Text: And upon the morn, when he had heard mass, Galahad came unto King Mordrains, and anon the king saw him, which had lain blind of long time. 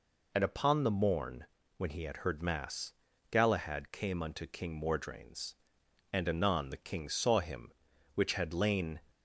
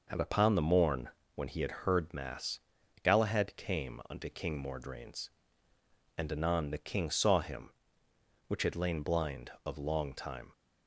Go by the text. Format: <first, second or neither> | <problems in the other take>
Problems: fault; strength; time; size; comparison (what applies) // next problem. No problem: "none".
second | stops before "blind of long time"; at 9.1 s